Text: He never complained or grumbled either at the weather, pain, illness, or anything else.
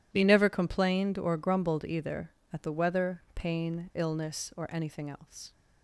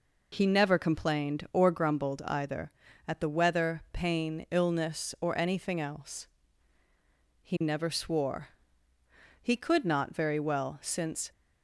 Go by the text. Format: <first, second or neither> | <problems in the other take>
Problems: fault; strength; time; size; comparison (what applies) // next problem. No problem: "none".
first | goes on to say "He never swore He could not very well since"; strong; from 7.4 s on; 3.8 s long